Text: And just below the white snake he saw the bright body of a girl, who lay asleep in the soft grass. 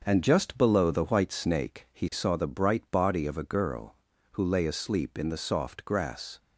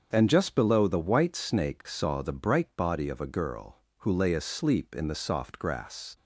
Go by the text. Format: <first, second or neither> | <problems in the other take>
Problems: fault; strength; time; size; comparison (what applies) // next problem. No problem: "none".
first | starts louder than the rest; strong; until 1.1 s; 7 dB; also in the first // skips "he"; at 1.8 s